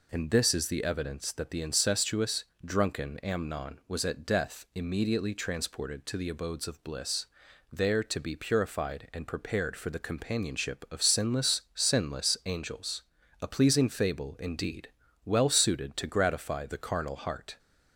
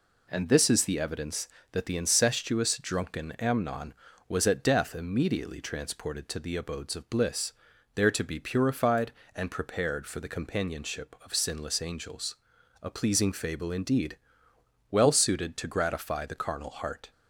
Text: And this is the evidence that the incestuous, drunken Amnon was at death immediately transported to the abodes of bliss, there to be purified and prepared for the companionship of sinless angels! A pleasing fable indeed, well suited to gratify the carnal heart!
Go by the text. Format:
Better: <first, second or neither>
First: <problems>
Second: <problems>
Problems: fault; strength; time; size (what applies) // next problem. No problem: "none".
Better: second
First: says "sinless" twice; at 11.7 s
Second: none